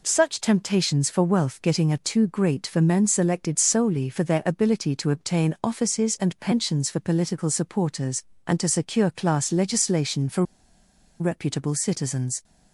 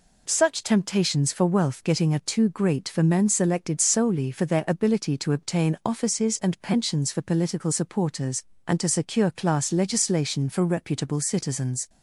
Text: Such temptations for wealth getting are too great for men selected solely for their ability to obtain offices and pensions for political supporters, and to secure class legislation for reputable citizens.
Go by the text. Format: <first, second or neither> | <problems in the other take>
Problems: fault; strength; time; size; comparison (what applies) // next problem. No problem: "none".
second | pauses between "for" and "reputable"; noticeable; at 10.4 s; 0.77 s long